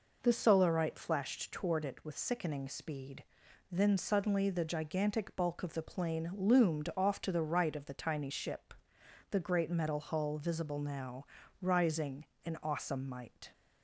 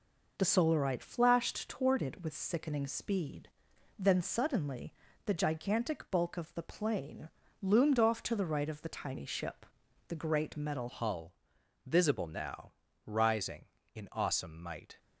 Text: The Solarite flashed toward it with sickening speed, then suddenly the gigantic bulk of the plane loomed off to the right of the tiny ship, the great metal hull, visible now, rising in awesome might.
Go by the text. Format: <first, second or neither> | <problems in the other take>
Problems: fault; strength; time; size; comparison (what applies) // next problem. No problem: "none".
first | pauses between "suddenly" and "the"; slight; at 4.9 s; 0.32 s long // pauses between "plane" and "loomed"; slight; at 7.2 s; 0.34 s long // changes voice at "hull"; from 10.8 s on; 4.1 s long